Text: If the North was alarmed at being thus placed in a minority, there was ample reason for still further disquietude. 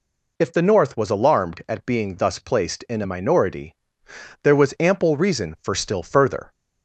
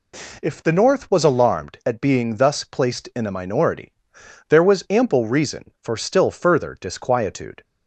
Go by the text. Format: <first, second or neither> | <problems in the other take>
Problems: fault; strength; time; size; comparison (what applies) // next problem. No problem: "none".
second | stops before "disquietude"; at 6.5 s